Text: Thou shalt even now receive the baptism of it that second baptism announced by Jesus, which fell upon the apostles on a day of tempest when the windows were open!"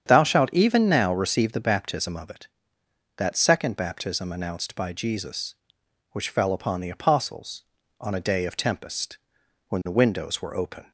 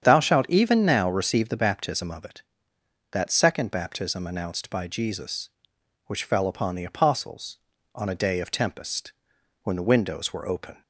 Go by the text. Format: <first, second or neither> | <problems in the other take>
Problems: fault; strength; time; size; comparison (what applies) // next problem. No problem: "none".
neither | starts louder than the rest; strong; the same in both // pauses between "tempest" and "when"; noticeable; the same in both